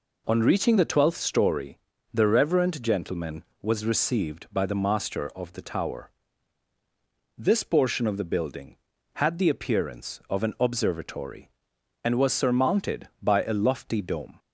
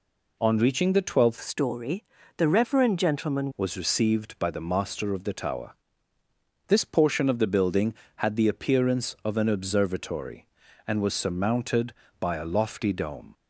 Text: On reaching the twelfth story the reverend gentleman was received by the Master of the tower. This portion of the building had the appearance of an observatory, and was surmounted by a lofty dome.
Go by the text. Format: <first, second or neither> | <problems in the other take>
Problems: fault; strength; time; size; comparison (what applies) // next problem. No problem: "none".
first | changes voice from "story" to "gentleman"; from 1.4 to 3.5 s; 2.1 s long // pauses between "story" and "the"; slight; at 2.0 s; 0.36 s long; slight in the first